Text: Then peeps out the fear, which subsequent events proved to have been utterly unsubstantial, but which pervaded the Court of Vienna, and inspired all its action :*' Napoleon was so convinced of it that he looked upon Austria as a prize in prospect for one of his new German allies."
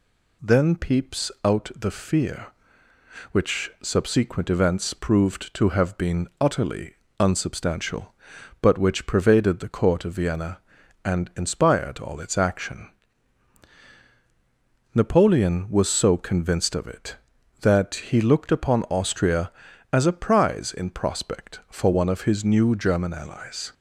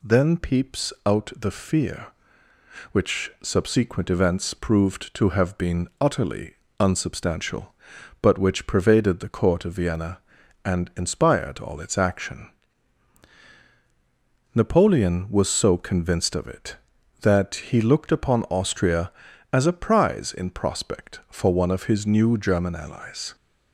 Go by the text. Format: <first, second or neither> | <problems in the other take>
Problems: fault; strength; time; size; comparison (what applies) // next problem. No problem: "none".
neither | pauses between "utterly" and "unsubstantial"; slight; the same in both